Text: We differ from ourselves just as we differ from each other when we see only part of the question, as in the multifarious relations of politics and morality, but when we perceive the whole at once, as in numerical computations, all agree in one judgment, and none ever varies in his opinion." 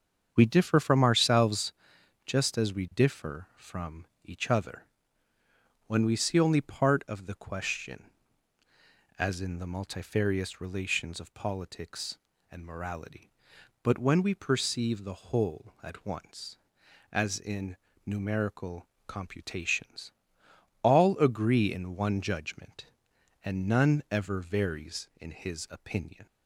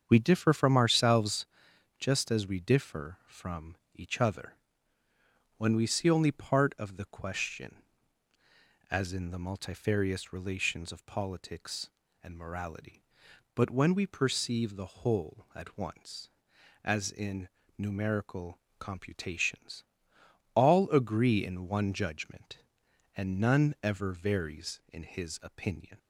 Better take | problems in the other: neither | starts louder than the rest; strong; the same in both // pauses between "ourselves" and "just"; noticeable; the same in both // pauses between "from" and "each"; slight; the same in both // pauses between "other" and "when"; the same in both // pauses between "in" and "numerical"; slight; the same in both // pauses between "numerical" and "computations"; slight; the same in both

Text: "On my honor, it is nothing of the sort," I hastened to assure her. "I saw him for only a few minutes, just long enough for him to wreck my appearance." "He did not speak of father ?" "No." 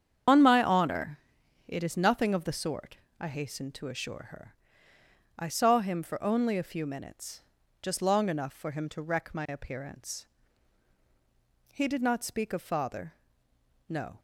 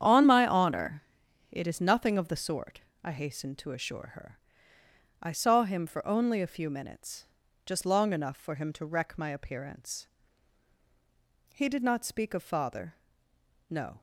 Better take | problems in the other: second | loses the start of "On"; at 0.2 s; 125 ms // starts louder than the rest; strong; until 1.7 s; 8.5 dB; strong in the second

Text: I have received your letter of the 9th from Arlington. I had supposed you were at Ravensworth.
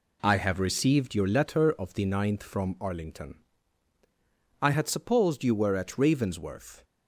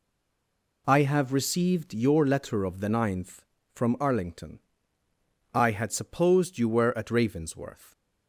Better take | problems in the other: first | stays silent before the first word; slight; until 0.8 s; 0.8 s long

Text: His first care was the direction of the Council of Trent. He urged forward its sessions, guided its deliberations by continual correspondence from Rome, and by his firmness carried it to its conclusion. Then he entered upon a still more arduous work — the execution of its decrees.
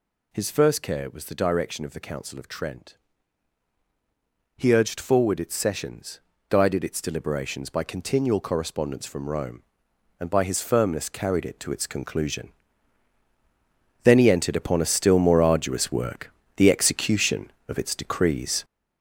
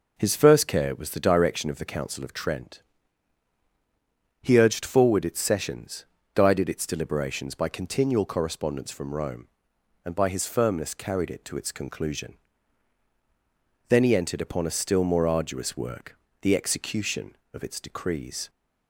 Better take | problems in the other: second | gets louder; throughout; 6.5 dB

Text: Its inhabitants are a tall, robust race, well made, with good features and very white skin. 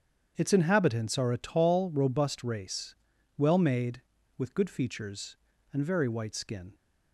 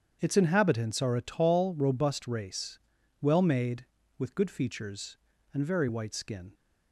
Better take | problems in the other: neither | starts louder than the rest; strong; the same in both

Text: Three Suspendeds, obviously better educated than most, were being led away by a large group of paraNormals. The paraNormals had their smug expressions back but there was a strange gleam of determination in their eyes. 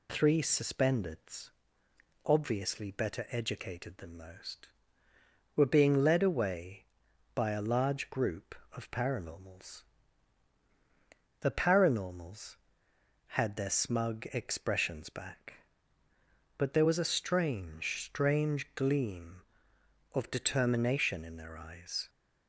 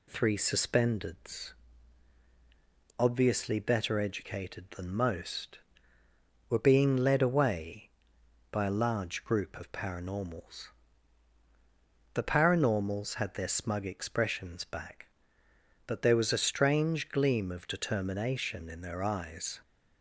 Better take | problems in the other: second | says "strange" twice; at 18.0 s

